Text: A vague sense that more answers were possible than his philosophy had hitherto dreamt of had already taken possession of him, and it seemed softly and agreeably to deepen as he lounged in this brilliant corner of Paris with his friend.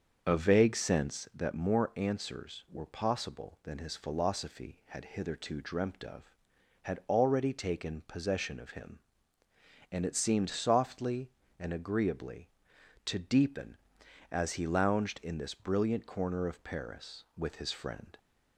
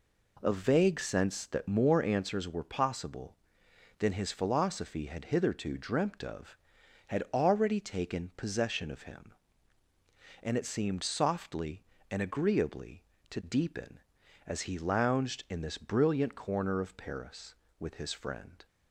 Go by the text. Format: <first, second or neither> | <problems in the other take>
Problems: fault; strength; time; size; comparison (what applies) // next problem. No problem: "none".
second | starts louder than the rest; until 1.5 s; 6.5 dB